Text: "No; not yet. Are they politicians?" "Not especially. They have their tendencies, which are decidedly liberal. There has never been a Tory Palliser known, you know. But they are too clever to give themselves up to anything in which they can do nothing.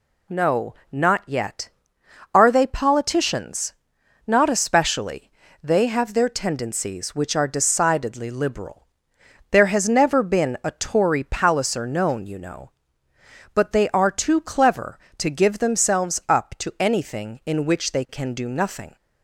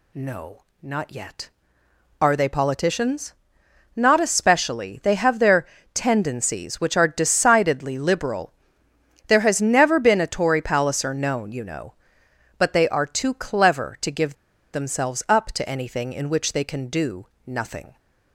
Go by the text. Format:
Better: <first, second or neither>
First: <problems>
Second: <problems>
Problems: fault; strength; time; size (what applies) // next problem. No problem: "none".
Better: first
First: none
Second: pauses between "their" and "tendencies"; slight; at 5.6 s; 0.26 s long // pauses between "give" and "themselves"; at 14.3 s; 0.41 s long // pauses between "do" and "nothing"; slight; at 17.2 s; 0.18 s long